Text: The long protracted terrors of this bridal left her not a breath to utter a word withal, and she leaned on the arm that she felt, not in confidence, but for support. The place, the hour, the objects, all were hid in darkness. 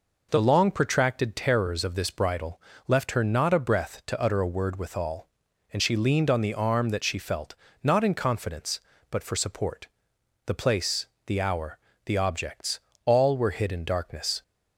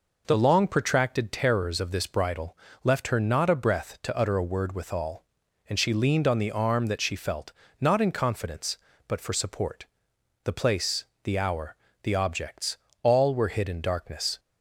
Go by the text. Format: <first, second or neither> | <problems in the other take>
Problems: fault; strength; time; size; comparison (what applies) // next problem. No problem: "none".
neither | pauses between "bridal" and "left"; slight; the same in both